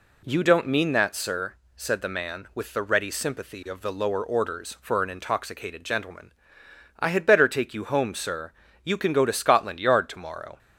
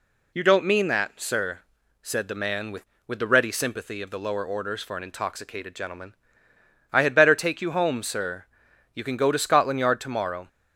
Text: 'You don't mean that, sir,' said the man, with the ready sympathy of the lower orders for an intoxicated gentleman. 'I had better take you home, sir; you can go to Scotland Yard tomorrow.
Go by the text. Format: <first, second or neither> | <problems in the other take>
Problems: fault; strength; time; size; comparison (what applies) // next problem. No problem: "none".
first | says "with" twice; at 3.0 s